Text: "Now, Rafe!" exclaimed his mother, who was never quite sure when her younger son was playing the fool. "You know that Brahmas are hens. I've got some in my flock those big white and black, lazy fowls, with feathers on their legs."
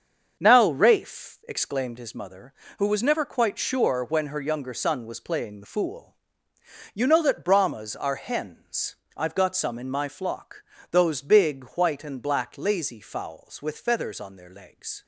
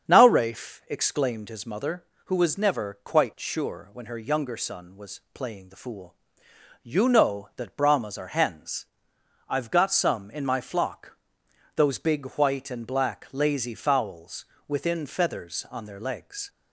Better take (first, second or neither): first